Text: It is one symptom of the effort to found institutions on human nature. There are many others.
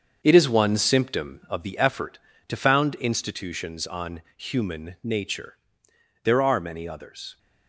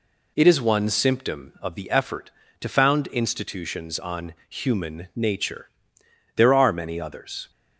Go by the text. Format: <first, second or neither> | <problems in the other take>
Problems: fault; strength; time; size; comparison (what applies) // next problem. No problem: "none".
second | gets quieter; strong; throughout; 8.5 dB